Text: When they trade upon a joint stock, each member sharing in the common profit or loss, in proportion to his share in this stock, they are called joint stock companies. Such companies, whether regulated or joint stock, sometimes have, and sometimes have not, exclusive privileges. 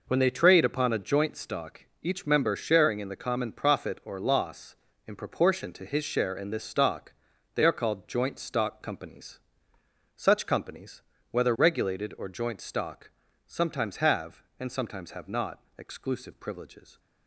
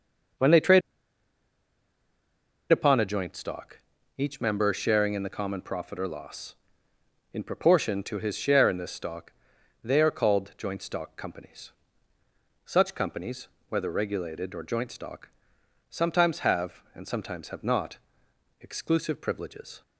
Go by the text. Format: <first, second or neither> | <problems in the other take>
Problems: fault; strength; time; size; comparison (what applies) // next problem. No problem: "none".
first | pauses between "trade" and "upon"; strong; at 0.8 s; 1.9 s long